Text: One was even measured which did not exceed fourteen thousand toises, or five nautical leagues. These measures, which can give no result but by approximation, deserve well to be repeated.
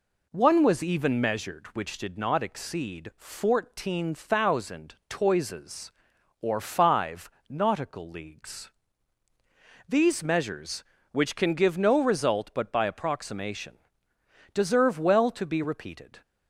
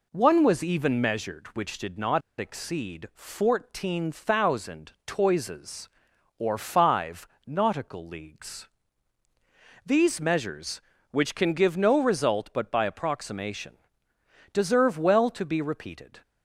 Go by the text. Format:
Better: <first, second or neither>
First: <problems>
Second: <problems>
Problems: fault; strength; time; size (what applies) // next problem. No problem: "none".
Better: first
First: pauses between "five" and "nautical"; slight; at 7.3 s; 0.18 s long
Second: pauses between "not" and "exceed"; slight; at 2.2 s; 0.18 s long // pauses between "five" and "nautical"; slight; at 7.2 s; 0.18 s long